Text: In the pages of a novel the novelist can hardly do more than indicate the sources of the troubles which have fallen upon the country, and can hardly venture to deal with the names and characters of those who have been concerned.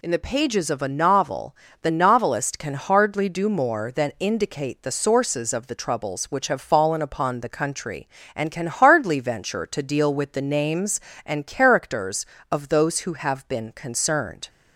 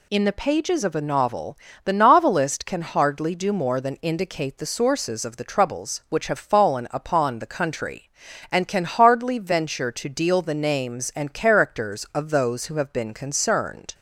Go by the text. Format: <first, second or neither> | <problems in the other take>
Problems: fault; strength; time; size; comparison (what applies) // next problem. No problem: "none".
first | pauses between "novel" and "the"; slight; at 1.5 s; 0.28 s long; slight in the first // skips "with"; at 10.4 s